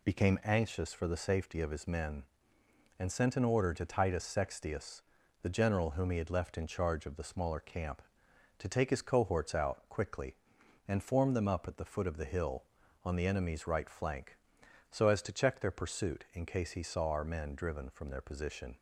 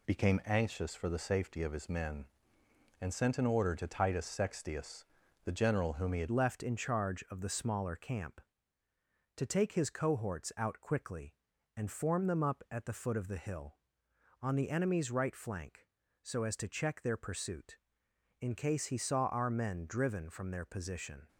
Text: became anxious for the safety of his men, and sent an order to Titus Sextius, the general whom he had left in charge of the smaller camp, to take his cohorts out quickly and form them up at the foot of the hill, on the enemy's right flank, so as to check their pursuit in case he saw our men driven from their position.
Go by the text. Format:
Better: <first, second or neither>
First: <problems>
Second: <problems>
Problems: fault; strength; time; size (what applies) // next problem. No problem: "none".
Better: first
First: none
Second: changes voice at "left"; from 6.2 s on; 15.0 s long